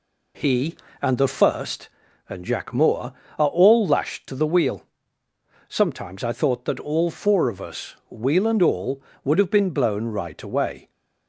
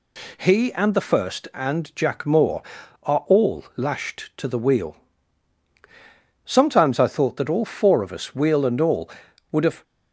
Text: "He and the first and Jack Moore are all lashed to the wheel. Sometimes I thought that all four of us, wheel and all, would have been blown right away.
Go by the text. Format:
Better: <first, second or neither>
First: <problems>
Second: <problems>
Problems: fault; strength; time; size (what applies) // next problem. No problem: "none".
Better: first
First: none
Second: stops before "been blown right away"; at 9.8 s